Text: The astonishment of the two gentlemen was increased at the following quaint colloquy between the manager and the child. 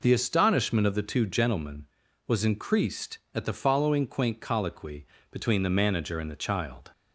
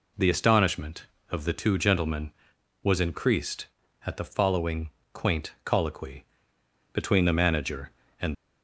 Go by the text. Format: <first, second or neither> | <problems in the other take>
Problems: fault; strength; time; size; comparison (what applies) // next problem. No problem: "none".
first | pauses between "following" and "quaint"; slight; at 4.8 s; 0.22 s long // pauses between "colloquy" and "between"; noticeable; at 6.2 s; 0.70 s long; slight in the first // stops before "the child"; at 8.3 s